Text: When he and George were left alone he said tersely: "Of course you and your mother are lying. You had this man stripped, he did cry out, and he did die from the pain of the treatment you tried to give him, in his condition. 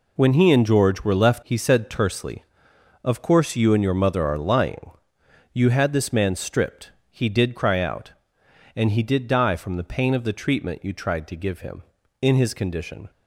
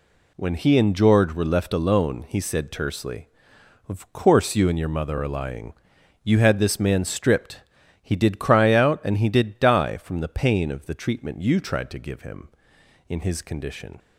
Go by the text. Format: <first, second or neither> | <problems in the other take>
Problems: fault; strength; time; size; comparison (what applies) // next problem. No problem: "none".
second | skips "alone"; at 1.4 s